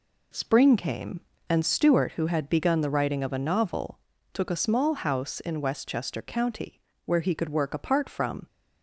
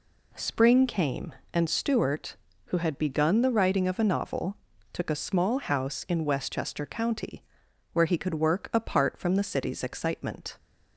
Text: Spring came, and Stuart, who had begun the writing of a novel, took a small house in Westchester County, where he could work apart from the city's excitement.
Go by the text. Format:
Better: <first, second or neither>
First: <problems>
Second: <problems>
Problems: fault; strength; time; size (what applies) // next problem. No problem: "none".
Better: second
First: stops before "the city's excitement"; at 8.4 s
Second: none